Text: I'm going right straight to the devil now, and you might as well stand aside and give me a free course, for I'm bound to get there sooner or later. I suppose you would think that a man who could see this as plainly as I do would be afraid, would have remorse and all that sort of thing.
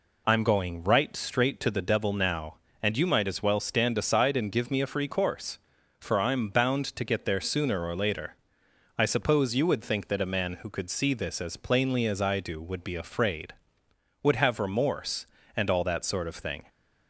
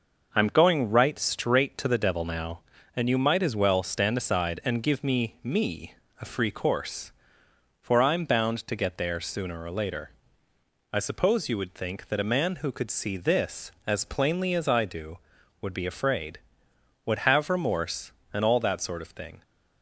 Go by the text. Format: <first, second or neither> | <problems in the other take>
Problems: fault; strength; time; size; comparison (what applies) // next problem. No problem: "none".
first | says "me" twice; at 5.4 s